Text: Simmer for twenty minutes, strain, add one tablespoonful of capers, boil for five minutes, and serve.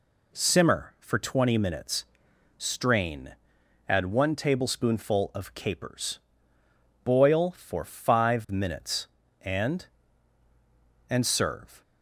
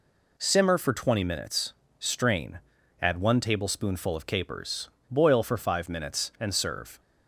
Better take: second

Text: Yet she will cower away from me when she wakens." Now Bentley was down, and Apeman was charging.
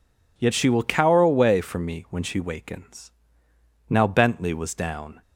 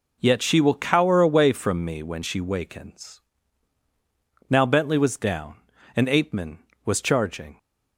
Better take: second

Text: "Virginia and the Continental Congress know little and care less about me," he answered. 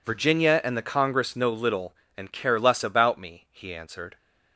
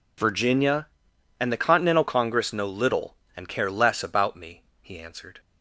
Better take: second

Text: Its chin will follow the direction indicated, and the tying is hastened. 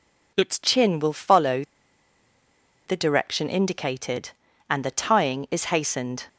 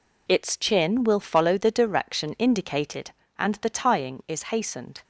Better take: second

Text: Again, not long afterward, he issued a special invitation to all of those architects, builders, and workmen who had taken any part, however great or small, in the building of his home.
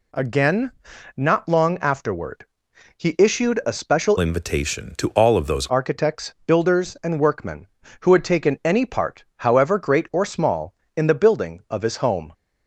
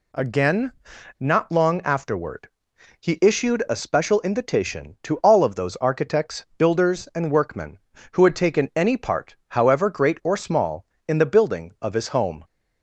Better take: second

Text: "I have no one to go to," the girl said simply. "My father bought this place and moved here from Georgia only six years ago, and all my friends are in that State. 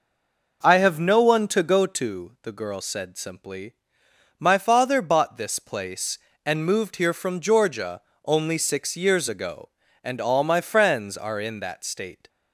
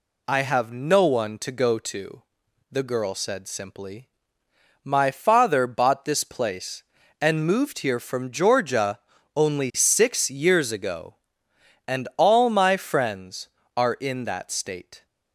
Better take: second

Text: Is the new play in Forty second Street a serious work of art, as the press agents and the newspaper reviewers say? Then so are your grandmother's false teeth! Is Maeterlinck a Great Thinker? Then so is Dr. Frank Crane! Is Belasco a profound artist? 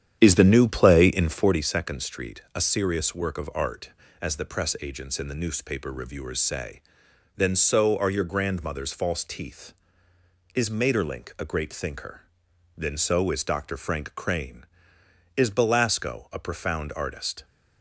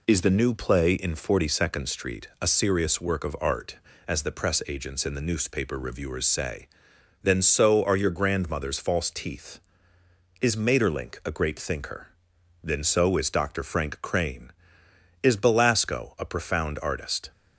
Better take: second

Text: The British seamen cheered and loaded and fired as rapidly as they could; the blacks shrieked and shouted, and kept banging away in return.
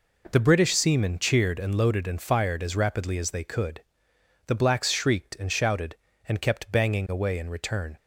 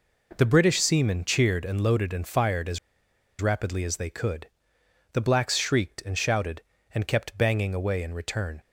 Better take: first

